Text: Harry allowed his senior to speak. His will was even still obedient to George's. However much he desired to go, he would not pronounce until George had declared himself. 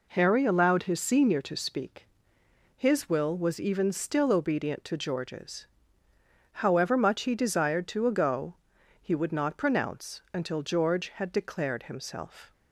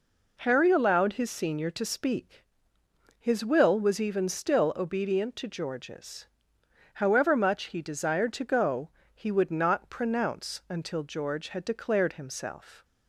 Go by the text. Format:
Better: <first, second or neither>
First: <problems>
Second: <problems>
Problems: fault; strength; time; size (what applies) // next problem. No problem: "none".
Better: second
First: says "ago" for "go"; at 8.0 s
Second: none